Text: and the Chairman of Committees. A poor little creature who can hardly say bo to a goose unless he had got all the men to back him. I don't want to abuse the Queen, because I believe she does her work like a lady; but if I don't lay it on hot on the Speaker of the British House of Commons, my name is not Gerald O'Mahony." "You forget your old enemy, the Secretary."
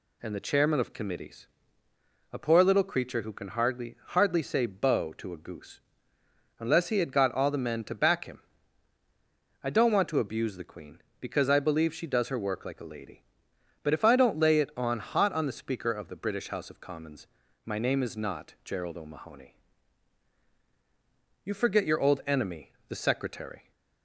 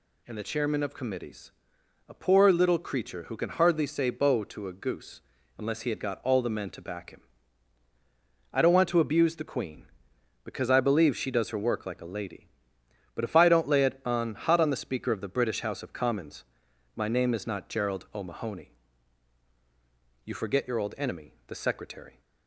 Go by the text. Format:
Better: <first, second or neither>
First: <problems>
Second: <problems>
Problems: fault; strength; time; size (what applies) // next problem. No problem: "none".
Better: second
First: says "hardly" twice; at 4.0 s // pauses between "goose" and "unless"; noticeable; at 5.8 s; 0.78 s long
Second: pauses between "goose" and "unless"; slight; at 5.2 s; 0.36 s long